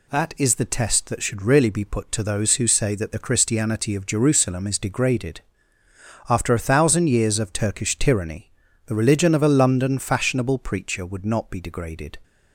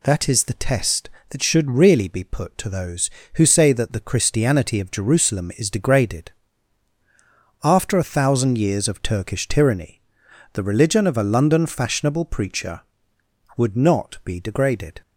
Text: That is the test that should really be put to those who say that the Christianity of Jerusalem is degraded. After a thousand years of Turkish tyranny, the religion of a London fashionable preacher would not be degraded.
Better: neither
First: none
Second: none

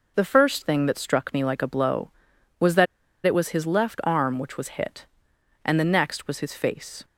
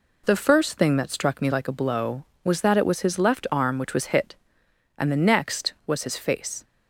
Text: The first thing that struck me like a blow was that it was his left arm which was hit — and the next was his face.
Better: second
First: pauses between "that" and "it"; at 2.8 s; 0.40 s long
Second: none

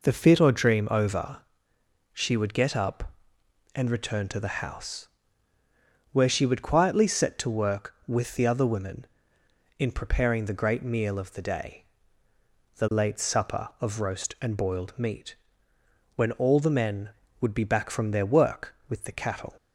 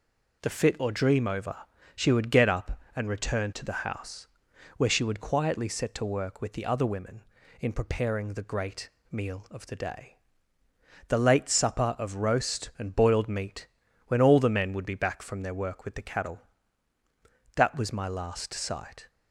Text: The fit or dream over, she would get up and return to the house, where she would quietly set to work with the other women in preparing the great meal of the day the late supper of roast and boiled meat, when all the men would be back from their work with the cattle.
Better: first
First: pauses between "day" and "the"; noticeable; at 11.8 s; 0.94 s long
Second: pauses between "great" and "meal"; slight; at 8.8 s; 0.22 s long // pauses between "day" and "the"; noticeable; at 10.1 s; 0.92 s long // goes on to say "That was my last sight"; from 17.5 s on; 1.5 s long

